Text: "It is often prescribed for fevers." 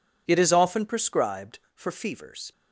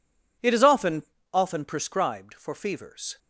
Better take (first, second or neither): first